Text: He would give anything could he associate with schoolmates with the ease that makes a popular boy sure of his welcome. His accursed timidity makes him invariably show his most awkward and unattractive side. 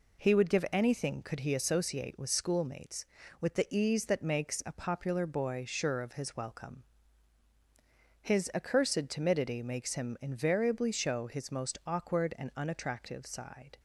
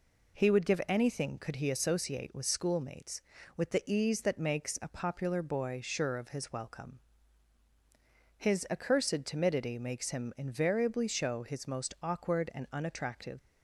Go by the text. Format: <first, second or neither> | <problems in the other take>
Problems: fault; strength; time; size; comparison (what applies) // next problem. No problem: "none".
first | stops before "side"; at 13.3 s